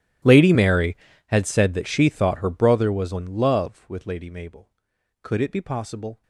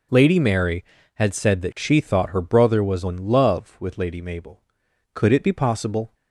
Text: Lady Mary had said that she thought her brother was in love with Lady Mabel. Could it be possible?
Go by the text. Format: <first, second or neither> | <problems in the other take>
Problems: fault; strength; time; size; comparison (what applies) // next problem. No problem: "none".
second | gets quieter; strong; throughout; 23 dB